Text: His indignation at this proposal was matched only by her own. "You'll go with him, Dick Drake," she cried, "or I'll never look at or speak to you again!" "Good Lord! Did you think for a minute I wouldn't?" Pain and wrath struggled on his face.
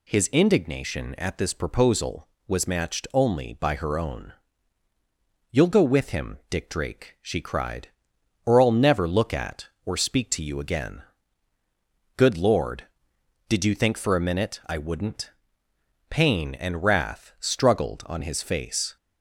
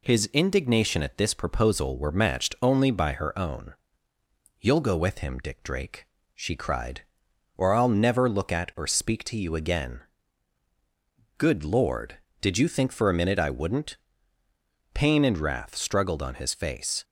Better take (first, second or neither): first